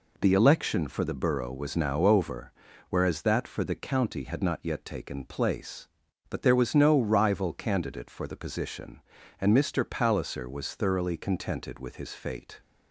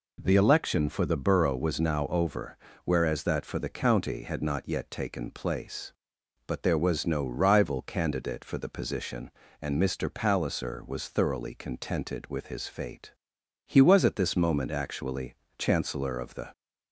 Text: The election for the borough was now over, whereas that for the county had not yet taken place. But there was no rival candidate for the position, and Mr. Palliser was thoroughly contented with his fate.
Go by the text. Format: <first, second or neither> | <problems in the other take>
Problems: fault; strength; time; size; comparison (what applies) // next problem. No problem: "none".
first | goes on to say "He was at this moment actually Chancellor of the"; strong; from 13.6 s on; 2.8 s long